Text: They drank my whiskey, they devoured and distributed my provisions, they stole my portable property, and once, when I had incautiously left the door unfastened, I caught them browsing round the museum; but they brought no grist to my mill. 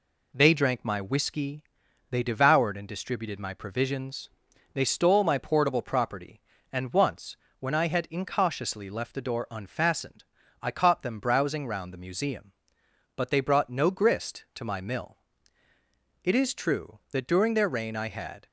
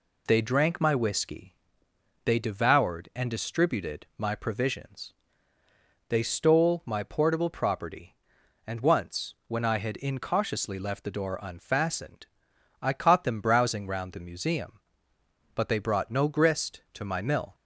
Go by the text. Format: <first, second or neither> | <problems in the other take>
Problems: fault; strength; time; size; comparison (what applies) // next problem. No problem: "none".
second | goes on to say "It is true that during their reign I had"; strong; from 16.2 s on; 2.2 s long